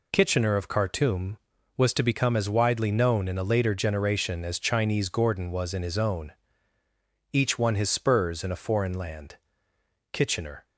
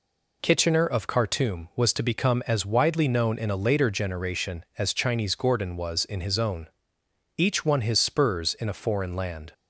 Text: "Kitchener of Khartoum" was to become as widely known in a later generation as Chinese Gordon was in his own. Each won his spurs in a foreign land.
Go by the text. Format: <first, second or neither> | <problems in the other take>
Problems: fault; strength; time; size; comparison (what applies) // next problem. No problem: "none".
second | goes on to say "Kitchener"; from 10.1 s on; 0.52 s long